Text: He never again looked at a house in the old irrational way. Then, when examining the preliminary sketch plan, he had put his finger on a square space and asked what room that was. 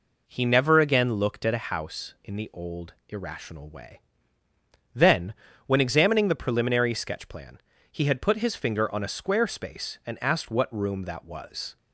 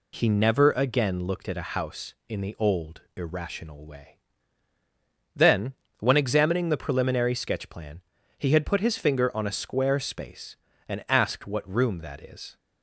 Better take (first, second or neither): first